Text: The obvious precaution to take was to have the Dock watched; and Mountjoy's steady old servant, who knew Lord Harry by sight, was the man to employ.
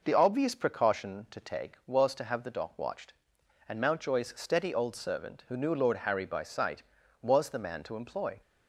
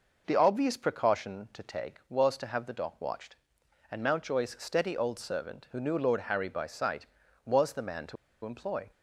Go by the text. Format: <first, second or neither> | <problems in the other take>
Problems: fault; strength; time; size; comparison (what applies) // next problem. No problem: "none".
first | pauses between "to" and "employ"; slight; at 8.1 s; 0.29 s long